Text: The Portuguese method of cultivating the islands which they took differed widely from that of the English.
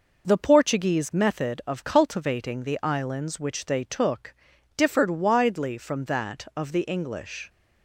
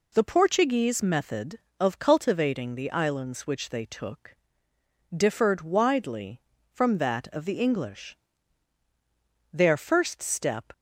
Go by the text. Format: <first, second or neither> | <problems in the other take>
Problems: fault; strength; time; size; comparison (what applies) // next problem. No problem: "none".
first | pauses between "took" and "differed"; noticeable; at 4.3 s; 0.82 s long; also in the first // goes on to say "Their first step"; noticeable; from 9.5 s on; 1.1 s long